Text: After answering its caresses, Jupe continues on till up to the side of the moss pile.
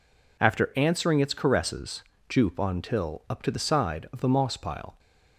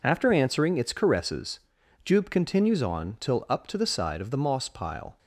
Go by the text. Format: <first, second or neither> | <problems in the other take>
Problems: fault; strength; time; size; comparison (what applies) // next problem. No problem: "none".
second | skips "continues"; at 2.5 s